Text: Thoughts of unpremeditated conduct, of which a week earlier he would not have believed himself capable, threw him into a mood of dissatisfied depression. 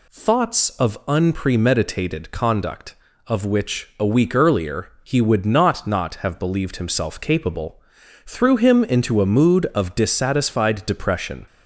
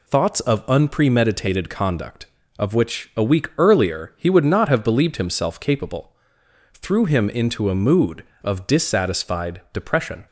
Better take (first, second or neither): second